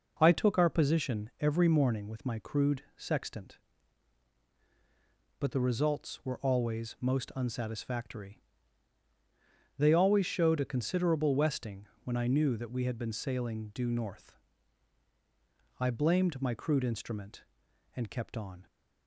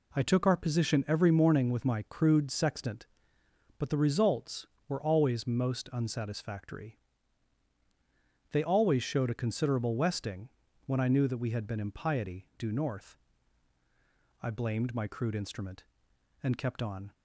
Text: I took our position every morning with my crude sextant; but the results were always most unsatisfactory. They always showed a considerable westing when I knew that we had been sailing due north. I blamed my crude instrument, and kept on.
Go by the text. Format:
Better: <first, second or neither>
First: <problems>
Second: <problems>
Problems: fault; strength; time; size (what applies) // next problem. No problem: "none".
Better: first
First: pauses between "westing" and "when"; slight; at 11.8 s; 0.18 s long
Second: pauses between "westing" and "when"; slight; at 10.4 s; 0.34 s long // says "impiety" for "sailing"; at 11.7 s